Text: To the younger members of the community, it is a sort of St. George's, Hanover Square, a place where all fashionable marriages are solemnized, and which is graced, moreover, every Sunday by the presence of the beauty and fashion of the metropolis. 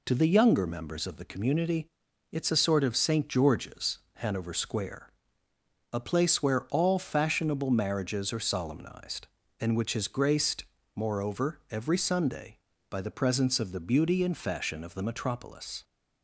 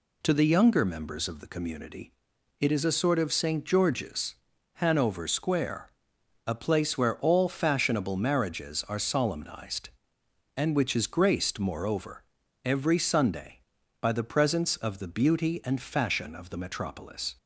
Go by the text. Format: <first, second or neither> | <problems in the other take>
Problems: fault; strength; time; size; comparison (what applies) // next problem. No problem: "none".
neither | none